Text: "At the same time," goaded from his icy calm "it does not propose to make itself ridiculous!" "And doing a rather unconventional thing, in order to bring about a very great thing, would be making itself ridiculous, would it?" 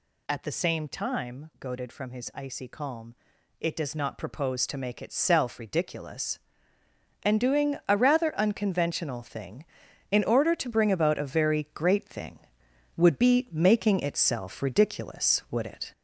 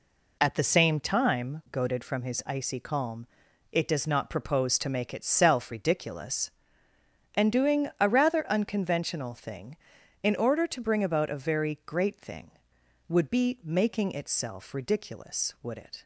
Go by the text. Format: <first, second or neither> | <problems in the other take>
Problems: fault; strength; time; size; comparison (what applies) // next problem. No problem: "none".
second | gets louder; noticeable; throughout; 5 dB // pauses between "calm" and "it"; noticeable; at 3.1 s; 0.46 s long; noticeable in the second